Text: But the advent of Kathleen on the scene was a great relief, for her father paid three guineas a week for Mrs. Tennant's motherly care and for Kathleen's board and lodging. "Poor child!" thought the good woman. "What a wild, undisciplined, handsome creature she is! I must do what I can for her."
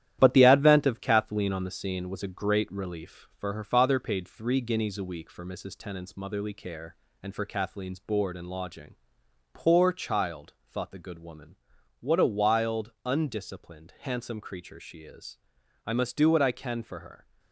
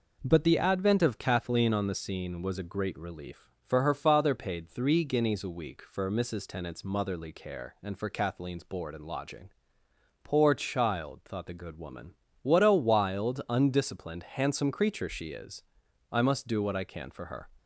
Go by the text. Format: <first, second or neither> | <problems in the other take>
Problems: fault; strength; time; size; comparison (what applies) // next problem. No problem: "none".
second | gets quieter; noticeable; throughout; 5.5 dB